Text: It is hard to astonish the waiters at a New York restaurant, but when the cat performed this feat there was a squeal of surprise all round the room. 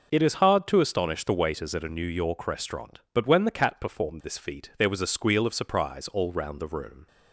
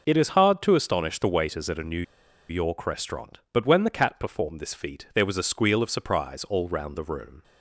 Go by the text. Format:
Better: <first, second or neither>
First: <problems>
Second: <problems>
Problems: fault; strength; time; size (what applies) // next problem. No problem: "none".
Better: first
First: none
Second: pauses between "New" and "York"; noticeable; at 2.0 s; 0.46 s long